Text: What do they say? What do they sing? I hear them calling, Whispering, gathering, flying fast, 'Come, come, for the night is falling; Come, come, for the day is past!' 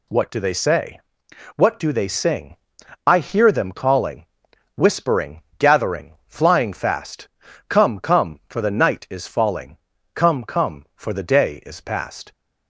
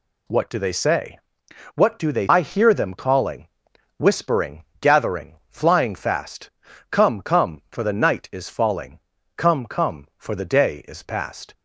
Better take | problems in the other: first | skips "sing"; at 2.2 s

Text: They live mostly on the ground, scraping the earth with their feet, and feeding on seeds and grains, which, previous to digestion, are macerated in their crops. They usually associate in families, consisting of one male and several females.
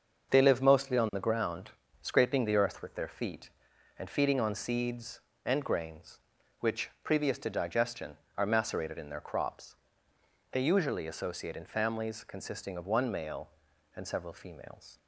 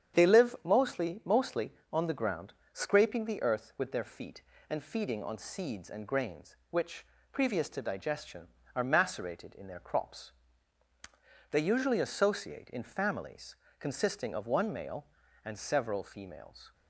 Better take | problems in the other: first | starts louder than the rest; strong; until 1.2 s; 8.5 dB; also in the first // says "mostly" twice; at 1.2 s

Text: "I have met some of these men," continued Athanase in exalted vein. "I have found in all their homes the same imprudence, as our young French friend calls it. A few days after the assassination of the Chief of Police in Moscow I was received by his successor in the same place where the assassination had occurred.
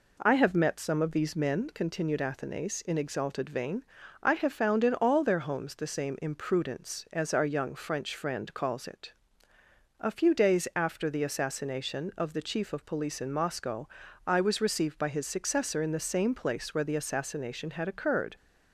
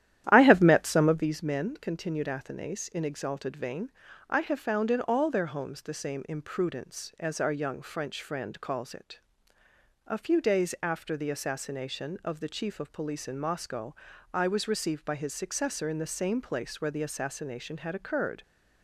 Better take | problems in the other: first | starts louder than the rest; strong; until 1.3 s; 12 dB // pauses between "Moscow" and "I"; at 13.9 s; 0.40 s long; also in the first

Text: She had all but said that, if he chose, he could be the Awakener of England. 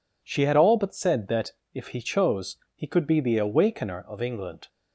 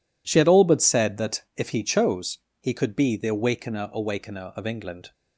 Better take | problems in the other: first | says "Awakener" twice; at 3.9 s

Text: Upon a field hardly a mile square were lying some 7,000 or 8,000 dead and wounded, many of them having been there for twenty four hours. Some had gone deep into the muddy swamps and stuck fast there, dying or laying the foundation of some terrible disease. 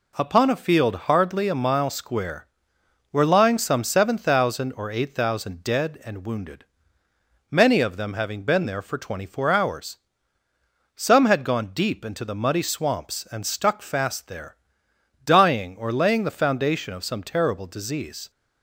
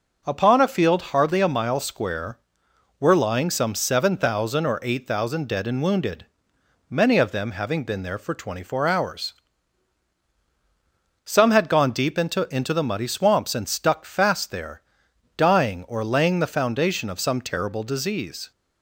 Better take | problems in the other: first | says "into" twice; at 12.5 s

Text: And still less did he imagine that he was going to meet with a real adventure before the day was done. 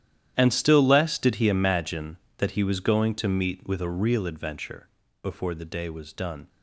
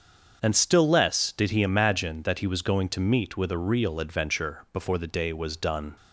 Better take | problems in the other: second | gets quieter; strong; throughout; 17.5 dB // starts louder than the rest; strong; until 1.3 s; 11.5 dB; also in the second // pauses between "adventure" and "before"; slight; at 4.8 s; 0.34 s long

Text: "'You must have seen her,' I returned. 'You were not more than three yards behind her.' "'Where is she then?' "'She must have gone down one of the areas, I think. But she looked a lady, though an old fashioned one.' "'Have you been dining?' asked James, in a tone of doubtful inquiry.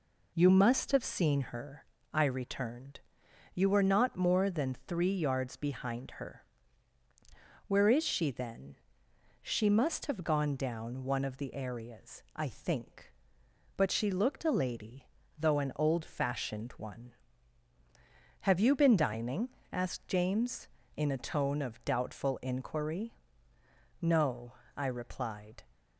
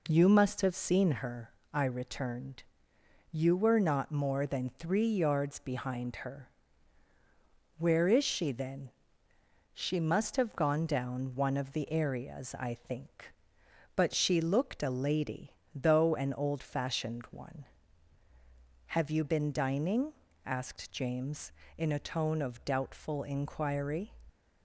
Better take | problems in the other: second | goes on to say "No I replied"; from 24.0 s on; 1.6 s long

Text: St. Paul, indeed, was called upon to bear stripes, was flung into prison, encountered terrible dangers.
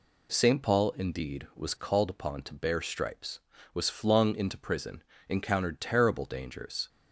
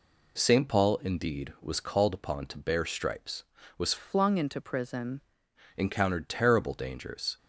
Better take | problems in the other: first | changes voice from "flung" to "prison"; from 3.9 to 5.2 s; 1.3 s long

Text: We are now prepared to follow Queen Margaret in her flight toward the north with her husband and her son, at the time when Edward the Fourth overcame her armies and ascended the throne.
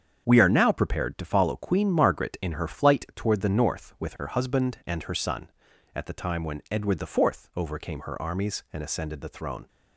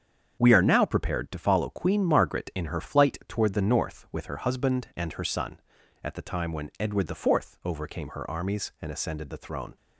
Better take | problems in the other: neither | starts louder than the rest; strong; the same in both

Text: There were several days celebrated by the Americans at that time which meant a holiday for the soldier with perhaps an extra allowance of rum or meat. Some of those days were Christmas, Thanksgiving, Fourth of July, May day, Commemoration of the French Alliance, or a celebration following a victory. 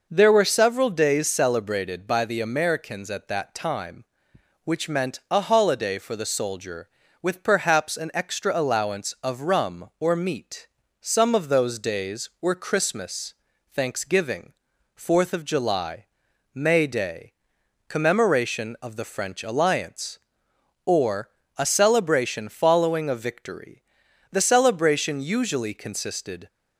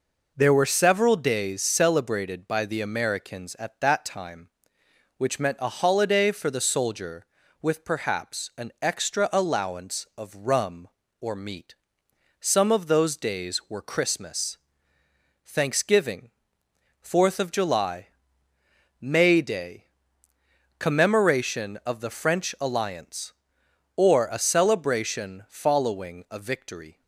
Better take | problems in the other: second | pauses between "or" and "a"; slight; at 21.2 s; 0.28 s long // goes on to say "The celebration usually consisted"; strong; from 24.3 s on; 2.1 s long

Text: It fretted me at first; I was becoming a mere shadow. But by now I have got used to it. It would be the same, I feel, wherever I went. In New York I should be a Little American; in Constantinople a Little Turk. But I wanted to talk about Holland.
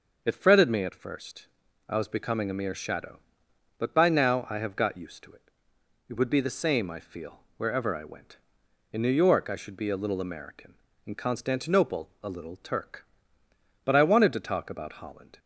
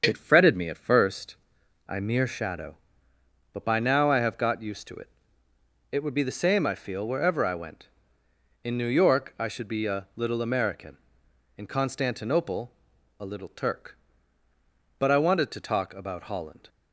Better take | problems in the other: first | starts louder than the rest; until 1.0 s; 7 dB; noticeable in the first // skips "was becoming a"; at 1.9 s // pauses between "Constantinople" and "a"; noticeable; at 12.7 s; 0.48 s long

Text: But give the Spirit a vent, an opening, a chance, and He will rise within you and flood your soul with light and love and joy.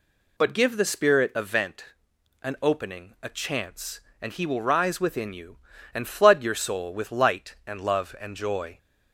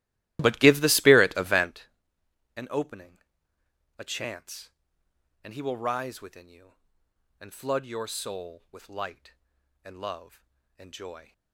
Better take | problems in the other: first | starts louder than the rest; strong; until 1.9 s; 15.5 dB

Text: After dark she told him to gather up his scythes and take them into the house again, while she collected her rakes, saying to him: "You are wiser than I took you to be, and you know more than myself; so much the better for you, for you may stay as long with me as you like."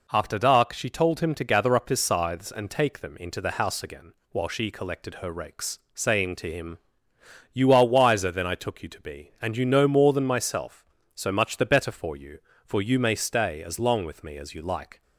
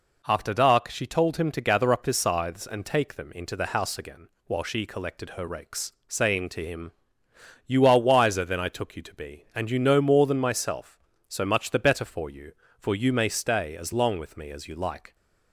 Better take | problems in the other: neither | none

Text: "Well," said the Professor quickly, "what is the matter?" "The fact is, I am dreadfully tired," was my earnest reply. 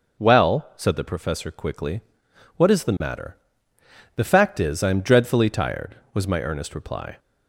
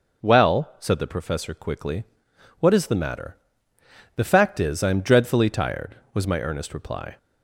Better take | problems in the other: neither | none

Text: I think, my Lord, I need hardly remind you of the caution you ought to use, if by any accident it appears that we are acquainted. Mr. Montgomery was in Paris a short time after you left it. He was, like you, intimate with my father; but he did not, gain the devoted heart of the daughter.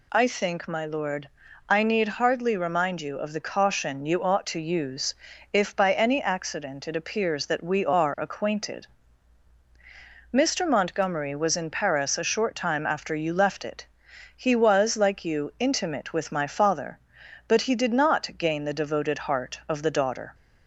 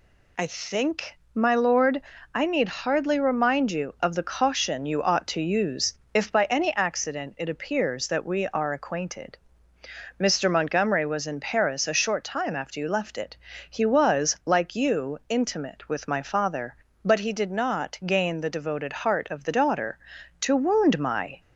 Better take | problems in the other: first | goes on to say "To wound my"; noticeable; from 20.4 s on; 0.98 s long

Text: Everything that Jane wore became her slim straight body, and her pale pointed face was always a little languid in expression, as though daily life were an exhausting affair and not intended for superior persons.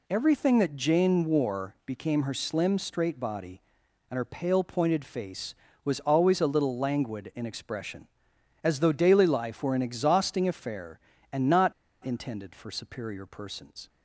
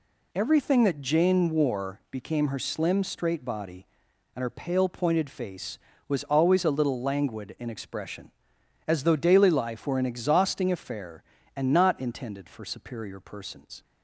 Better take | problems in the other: second | pauses between "not" and "intended"; slight; at 11.7 s; 0.31 s long

